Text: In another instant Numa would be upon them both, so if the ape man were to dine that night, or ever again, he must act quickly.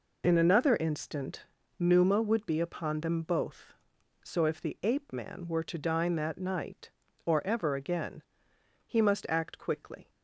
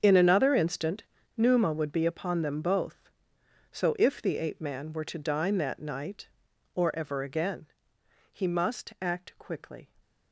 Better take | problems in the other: first | gets quieter; strong; throughout; 16 dB // pauses between "instant" and "Numa"; slight; at 1.0 s; 0.32 s long; slight in the first

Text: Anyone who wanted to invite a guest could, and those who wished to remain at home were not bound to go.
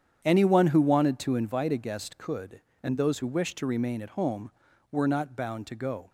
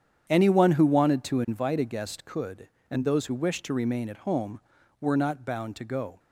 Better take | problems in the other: neither | starts louder than the rest; strong; the same in both

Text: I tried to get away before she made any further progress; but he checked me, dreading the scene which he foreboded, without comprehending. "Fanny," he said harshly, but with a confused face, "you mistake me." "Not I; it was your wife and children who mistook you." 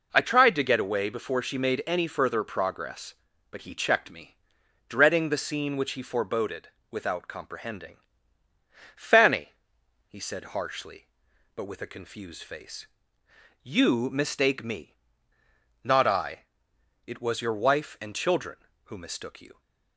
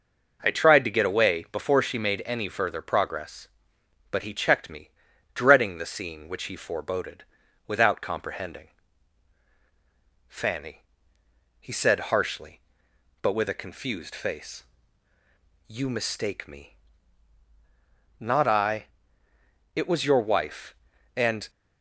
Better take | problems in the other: first | stops before "children who mistook you"; at 21.4 s

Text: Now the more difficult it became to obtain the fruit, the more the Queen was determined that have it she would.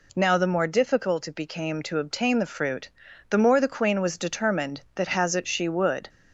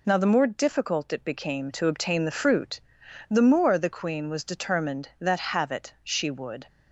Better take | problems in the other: second | says "has" for "have"; at 5.0 s

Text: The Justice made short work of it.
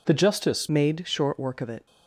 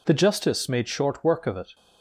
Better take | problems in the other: second | changes voice at "made"; from 0.6 s on; 1.2 s long

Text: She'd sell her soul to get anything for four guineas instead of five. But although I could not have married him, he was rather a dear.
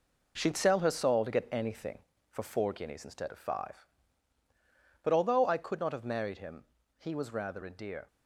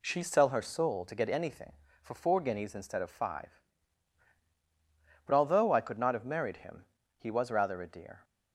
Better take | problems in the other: second | gets quieter; strong; throughout; 8.5 dB

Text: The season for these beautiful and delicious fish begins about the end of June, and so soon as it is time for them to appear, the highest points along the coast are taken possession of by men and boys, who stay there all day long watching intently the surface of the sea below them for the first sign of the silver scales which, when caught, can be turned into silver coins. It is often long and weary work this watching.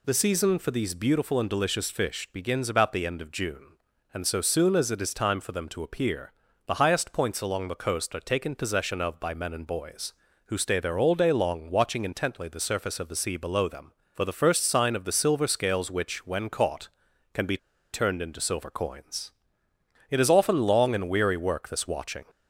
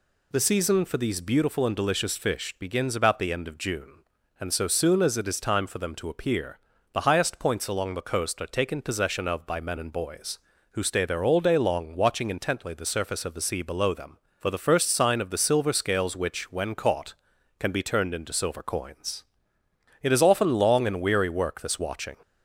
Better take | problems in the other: second | pauses between "be" and "turned"; slight; at 17.5 s; 0.35 s long

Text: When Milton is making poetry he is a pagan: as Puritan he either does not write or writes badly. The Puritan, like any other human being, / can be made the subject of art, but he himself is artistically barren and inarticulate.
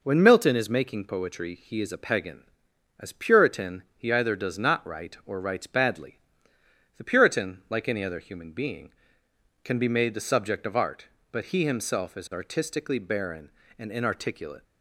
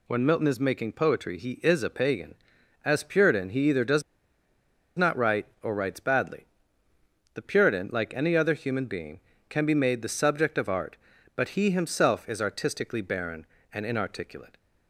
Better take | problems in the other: first | pauses between "does" and "not"; noticeable; at 4.0 s; 0.95 s long

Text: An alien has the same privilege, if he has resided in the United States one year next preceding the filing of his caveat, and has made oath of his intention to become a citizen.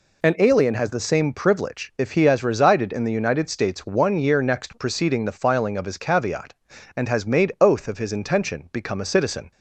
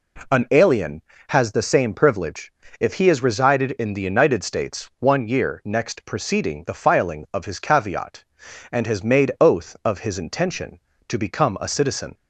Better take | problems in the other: second | skips "to"; at 8.7 s

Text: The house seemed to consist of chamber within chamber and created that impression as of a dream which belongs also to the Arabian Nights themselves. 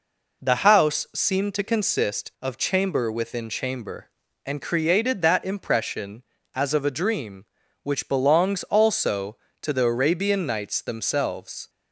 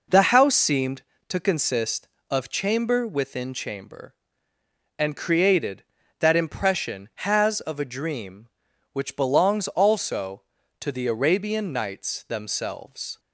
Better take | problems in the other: first | says "has" for "as"; at 7.1 s

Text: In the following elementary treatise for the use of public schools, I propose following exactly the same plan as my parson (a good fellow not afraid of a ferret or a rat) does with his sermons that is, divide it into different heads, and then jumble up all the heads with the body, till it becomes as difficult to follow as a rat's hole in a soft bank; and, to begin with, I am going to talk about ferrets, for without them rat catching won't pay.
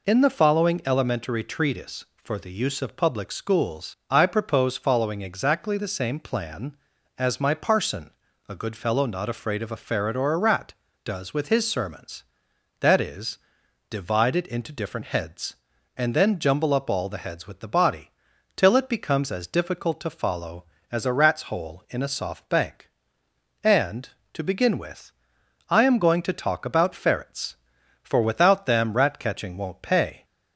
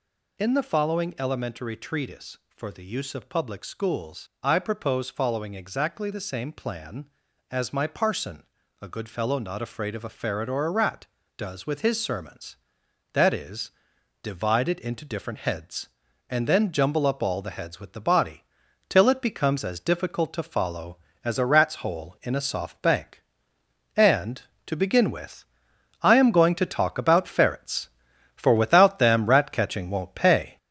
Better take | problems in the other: first | gets louder; noticeable; throughout; 5 dB

